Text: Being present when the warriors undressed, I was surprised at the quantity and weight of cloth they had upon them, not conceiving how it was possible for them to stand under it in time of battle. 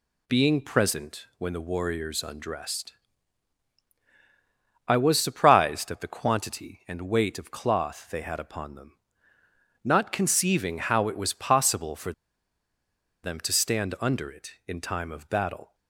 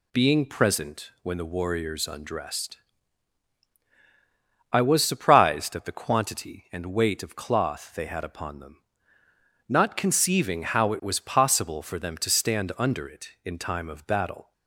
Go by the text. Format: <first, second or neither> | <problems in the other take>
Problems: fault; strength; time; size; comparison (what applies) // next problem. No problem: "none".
second | pauses between "for" and "them"; at 12.1 s; 1.1 s long